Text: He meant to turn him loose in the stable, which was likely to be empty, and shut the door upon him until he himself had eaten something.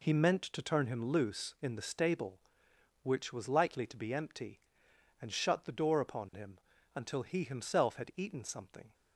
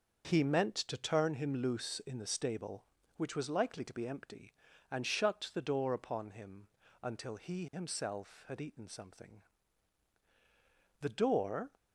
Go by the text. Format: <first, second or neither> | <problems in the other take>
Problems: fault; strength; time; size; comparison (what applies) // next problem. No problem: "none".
first | starts louder than the rest; until 1.4 s; 6.5 dB // pauses between "him" and "until"; slight; at 6.6 s; 0.34 s long; slight in the first // goes on to say "The door"; noticeable; from 11.0 s on; 0.70 s long